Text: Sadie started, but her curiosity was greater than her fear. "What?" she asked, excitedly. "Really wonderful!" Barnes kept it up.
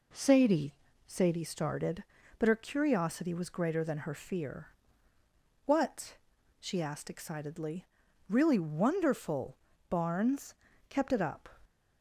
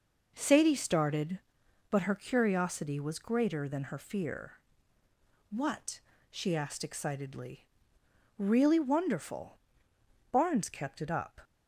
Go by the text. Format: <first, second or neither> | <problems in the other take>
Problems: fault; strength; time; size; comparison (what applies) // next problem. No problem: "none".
second | says "Sadie" twice; at 1.0 s // pauses between "Barnes" and "kept"; slight; at 10.5 s; 0.36 s long